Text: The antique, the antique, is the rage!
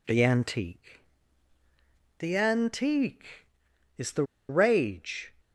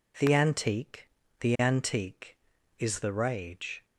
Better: second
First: pauses between "the" and "rage"; slight; at 4.2 s; 0.25 s long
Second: none

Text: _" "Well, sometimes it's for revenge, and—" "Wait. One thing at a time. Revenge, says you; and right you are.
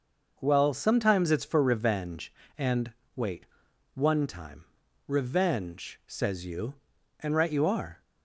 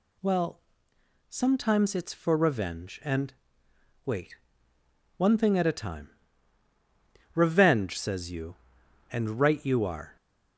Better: second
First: skips "thing at a"; at 4.2 s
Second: none

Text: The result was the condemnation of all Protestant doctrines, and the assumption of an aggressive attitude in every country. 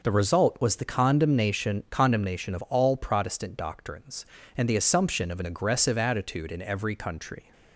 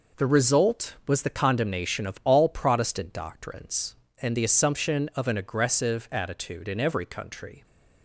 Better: second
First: says "condemnation" twice; at 1.9 s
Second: none

